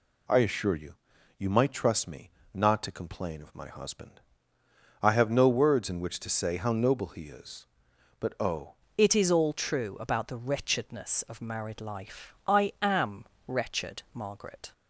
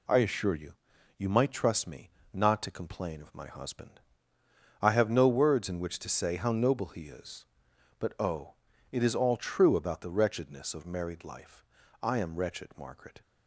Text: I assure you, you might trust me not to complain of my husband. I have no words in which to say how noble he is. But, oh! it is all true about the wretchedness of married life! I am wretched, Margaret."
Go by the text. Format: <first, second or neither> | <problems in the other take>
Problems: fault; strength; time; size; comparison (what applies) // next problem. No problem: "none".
second | pauses between "me" and "not"; slight; at 2.3 s; 0.22 s long; slight in the second // changes voice at "it"; from 8.9 s on; 5.8 s long // pauses between "am" and "wretched"; slight; at 13.2 s; 0.22 s long